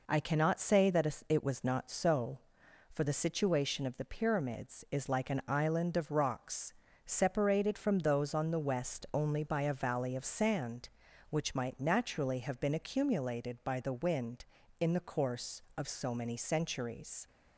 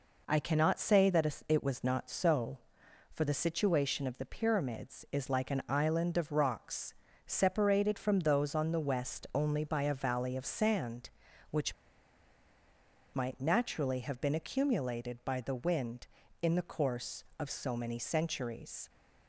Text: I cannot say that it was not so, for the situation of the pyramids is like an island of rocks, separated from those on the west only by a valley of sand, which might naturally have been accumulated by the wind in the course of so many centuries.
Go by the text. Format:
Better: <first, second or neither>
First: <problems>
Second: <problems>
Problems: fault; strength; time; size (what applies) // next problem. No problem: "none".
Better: first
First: none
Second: pauses between "which" and "might"; strong; at 11.7 s; 1.4 s long